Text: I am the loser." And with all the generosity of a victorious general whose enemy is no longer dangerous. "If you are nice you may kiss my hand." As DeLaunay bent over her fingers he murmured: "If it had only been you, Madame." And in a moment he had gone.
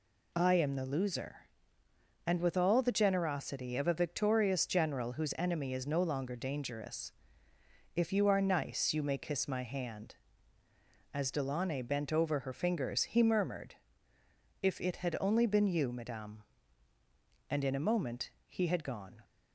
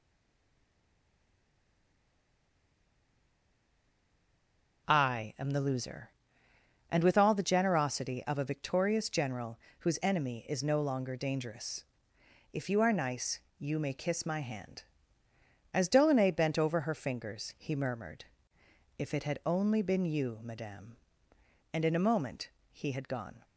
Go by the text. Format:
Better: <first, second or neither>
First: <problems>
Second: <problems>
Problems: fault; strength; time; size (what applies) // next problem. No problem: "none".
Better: first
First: pauses between "moment" and "he"; slight; at 18.2 s; 0.16 s long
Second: stays silent before the first word; strong; until 4.8 s; 4.8 s long // pauses between "general" and "whose"; slight; at 9.5 s; 0.20 s long // pauses between "nice" and "you"; slight; at 13.3 s; 0.18 s long // pauses between "moment" and "he"; slight; at 22.4 s; 0.20 s long